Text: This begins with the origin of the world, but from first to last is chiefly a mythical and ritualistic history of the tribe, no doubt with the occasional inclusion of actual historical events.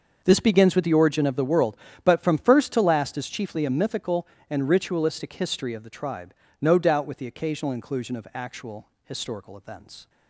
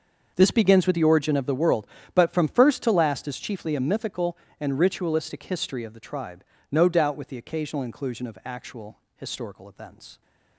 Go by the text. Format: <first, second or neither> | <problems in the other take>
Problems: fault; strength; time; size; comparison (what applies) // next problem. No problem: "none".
neither | starts louder than the rest; the same in both // pauses between "actual" and "historical"; slight; the same in both